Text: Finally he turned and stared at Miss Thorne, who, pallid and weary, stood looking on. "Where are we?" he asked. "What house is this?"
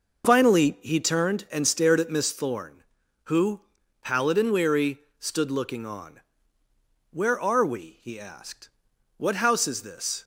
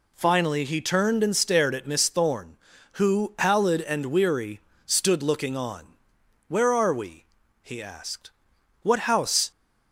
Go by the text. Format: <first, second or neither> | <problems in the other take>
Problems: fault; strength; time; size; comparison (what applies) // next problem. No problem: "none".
first | stops before "is this"; at 9.5 s